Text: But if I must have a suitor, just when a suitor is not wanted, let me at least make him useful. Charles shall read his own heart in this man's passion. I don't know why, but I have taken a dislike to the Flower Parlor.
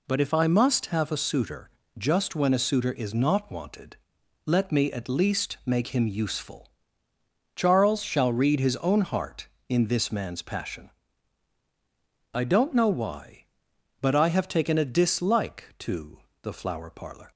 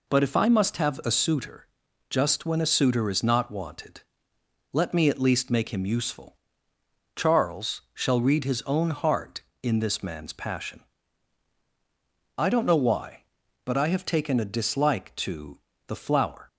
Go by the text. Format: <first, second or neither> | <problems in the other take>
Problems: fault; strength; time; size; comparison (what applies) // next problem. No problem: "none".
first | pauses between "to" and "the"; slight; at 15.5 s; 0.30 s long; slight in the first // stops before "Parlor"; at 16.4 s